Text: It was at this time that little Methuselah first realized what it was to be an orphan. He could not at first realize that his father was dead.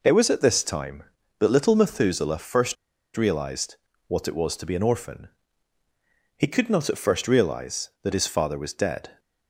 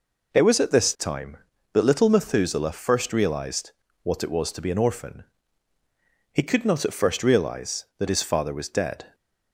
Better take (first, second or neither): second